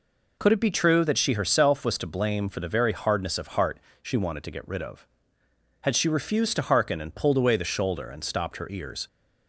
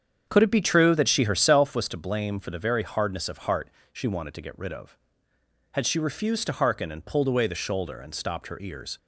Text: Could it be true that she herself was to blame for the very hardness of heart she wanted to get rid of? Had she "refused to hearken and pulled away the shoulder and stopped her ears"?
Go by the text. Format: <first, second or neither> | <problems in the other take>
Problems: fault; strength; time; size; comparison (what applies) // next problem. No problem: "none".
first | starts louder than the rest; strong; until 1.9 s; 8 dB // pauses between "heart" and "she"; slight; at 3.6 s; 0.24 s long; slight in the first